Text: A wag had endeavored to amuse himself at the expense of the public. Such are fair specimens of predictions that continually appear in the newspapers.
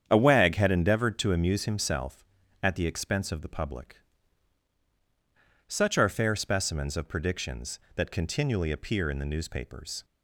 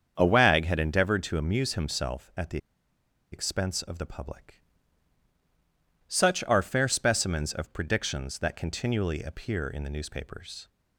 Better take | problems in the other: first | starts louder than the rest; strong; until 1.1 s; 7.5 dB; strong in the first // pauses between "the" and "expense"; noticeable; at 2.5 s; 0.74 s long

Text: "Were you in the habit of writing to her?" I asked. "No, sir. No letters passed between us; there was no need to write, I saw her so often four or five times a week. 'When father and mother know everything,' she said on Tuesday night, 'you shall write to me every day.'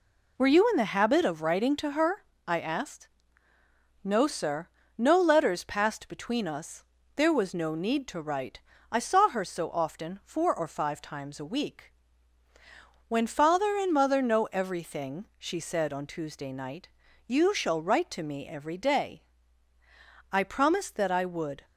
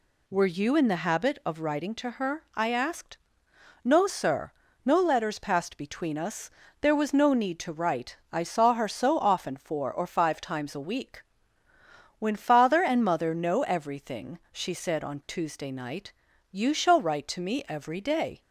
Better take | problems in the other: second | goes on to say "I promised that I would"; from 20.3 s on; 1.3 s long

